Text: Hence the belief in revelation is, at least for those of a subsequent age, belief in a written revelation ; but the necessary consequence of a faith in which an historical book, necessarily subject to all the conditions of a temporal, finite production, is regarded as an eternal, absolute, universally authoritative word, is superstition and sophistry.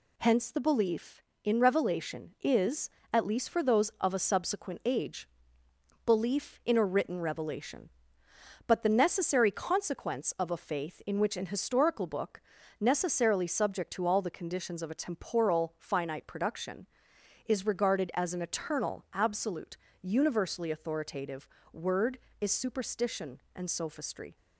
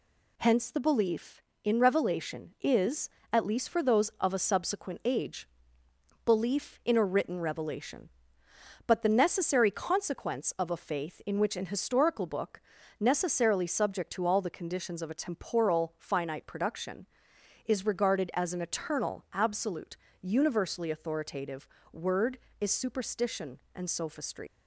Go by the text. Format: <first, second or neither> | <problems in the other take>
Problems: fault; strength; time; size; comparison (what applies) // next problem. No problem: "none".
first | pauses between "authoritative" and "word"; slight; at 21.6 s; 0.24 s long; slight in the first // leaves "sophistry" unfinished; at 24.4 s; 85 ms